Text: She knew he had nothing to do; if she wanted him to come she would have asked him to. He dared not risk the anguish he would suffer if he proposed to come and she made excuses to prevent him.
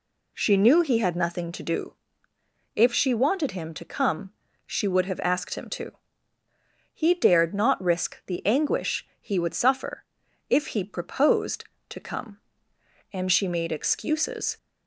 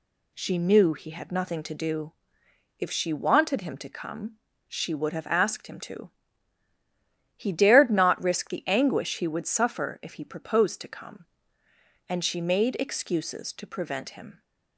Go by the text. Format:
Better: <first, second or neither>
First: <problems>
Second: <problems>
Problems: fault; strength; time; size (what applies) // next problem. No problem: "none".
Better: second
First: pauses between "come" and "she"; slight; at 4.3 s; 0.34 s long // pauses between "suffer" and "if"; noticeable; at 10.0 s; 0.46 s long // stops before "to prevent him"; at 14.5 s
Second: pauses between "come" and "she"; slight; at 4.3 s; 0.30 s long